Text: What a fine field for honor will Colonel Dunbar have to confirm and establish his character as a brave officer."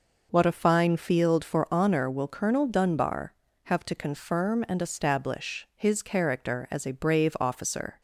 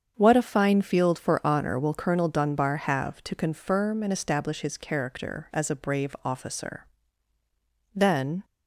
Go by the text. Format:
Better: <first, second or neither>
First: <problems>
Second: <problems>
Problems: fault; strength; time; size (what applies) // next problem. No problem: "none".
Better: first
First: none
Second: starts louder than the rest; strong; until 1.1 s; 7.5 dB // goes on to say "Then"; from 7.9 s on; 0.52 s long